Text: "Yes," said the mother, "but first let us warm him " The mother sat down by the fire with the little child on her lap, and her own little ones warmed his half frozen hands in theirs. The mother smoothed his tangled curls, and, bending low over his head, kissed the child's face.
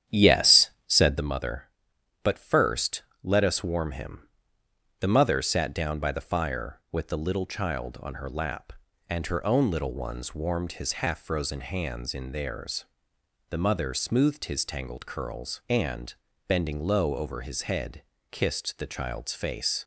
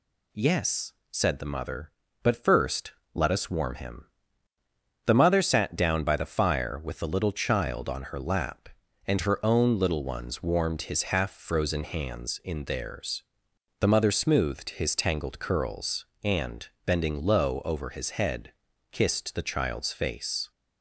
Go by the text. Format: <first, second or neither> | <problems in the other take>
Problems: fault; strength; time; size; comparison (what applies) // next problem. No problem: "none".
second | starts louder than the rest; strong; until 1.3 s; 9.5 dB // pauses between "first" and "let"; slight; at 3.0 s; 0.22 s long; slight in the second